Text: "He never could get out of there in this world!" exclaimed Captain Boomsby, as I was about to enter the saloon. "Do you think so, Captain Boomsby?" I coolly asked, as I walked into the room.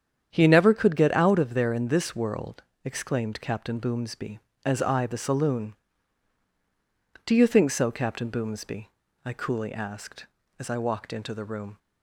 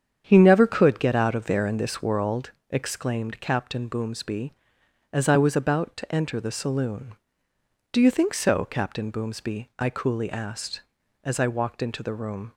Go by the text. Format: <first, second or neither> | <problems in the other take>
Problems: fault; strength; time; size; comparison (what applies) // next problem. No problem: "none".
second | starts louder than the rest; strong; until 1.3 s; 8.5 dB; strong in the second // skips "was about to enter"; at 5.0 s